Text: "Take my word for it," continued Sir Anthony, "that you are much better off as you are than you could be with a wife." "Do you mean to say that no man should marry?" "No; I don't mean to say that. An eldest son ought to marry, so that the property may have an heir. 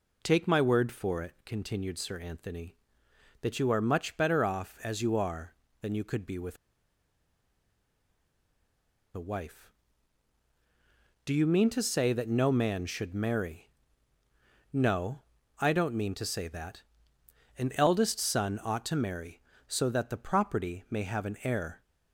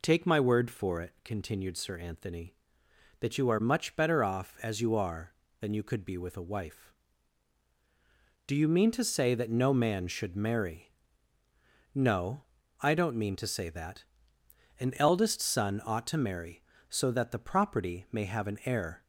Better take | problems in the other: second | pauses between "with" and "a"; strong; at 6.5 s; 2.5 s long

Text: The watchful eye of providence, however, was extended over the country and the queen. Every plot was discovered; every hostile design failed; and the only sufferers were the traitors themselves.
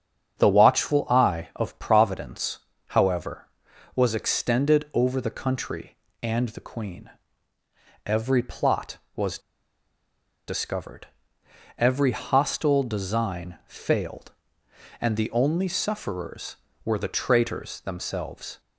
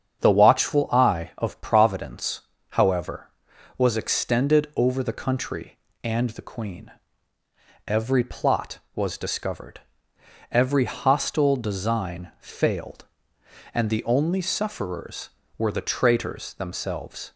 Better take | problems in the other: second | starts louder than the rest; strong; until 1.4 s; 7.5 dB; strong in the second // pauses between "was" and "discovered"; at 9.3 s; 1.0 s long

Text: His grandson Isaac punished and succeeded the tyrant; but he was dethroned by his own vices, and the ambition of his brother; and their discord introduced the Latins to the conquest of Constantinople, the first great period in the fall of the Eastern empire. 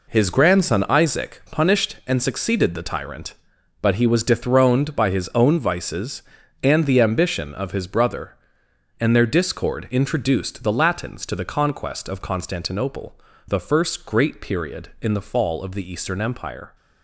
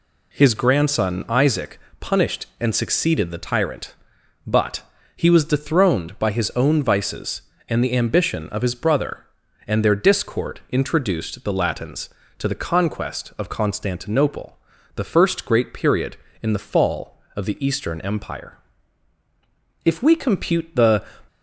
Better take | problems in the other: first | pauses between "Isaac" and "punished"; slight; at 1.7 s; 0.20 s long // pauses between "but" and "he"; slight; at 4.8 s; 0.36 s long // goes on to say "If we compute the"; noticeable; from 19.8 s on; 1.2 s long

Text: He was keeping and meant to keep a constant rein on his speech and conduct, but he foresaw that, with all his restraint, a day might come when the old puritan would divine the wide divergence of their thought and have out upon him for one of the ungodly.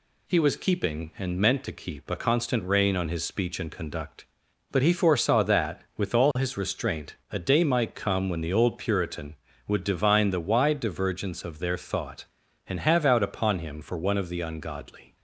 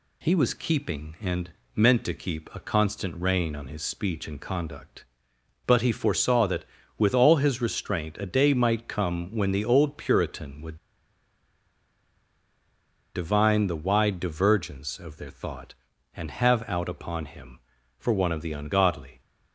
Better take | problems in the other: first | pauses between "and" and "meant"; slight; at 1.4 s; 0.24 s long // pauses between "would" and "divine"; strong; at 10.7 s; 2.3 s long

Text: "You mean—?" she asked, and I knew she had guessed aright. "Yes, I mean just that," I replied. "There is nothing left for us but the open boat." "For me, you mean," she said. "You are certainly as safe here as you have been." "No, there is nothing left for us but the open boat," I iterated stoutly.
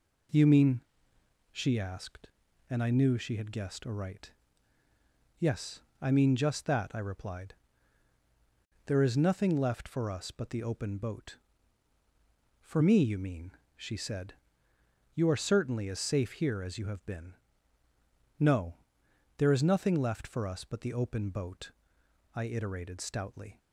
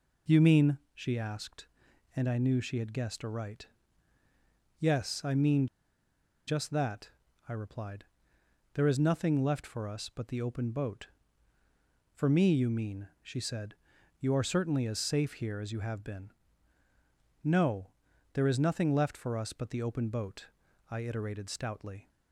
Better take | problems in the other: first | pauses between "mean" and "just"; noticeable; at 5.6 s; 0.80 s long

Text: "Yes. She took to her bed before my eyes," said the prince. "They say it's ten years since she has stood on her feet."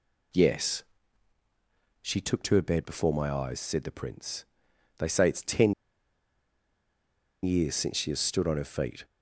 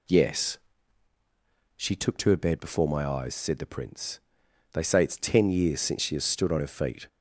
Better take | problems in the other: second | pauses between "ten" and "years"; strong; at 5.7 s; 1.6 s long

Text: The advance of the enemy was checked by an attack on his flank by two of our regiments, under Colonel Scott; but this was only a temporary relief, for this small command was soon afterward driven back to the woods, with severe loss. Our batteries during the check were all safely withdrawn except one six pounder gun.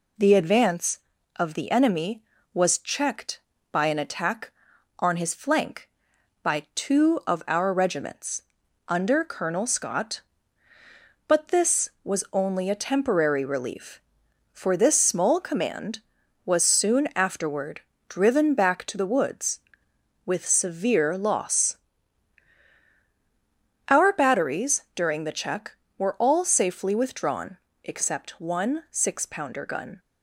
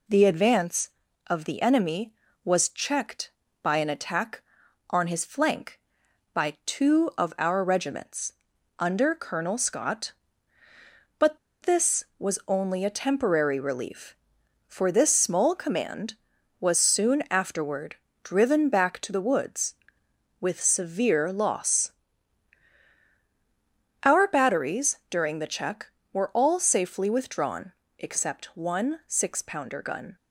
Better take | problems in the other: first | pauses between "but" and "this"; slight; at 11.3 s; 0.25 s long // pauses between "afterward" and "driven"; slight; at 17.9 s; 0.26 s long; slight in the first // pauses between "withdrawn" and "except"; slight; at 27.7 s; 0.30 s long; slight in the first

